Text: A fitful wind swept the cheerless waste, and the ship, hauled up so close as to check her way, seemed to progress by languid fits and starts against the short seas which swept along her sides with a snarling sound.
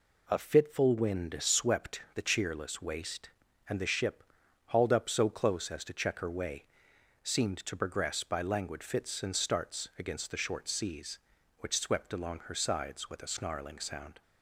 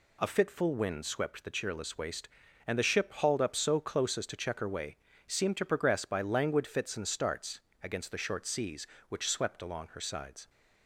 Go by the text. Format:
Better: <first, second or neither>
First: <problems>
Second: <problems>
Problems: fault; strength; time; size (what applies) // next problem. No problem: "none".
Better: first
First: none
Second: pauses between "starts" and "against"; slight; at 7.6 s; 0.20 s long // stops before "with a snarling sound"; at 10.4 s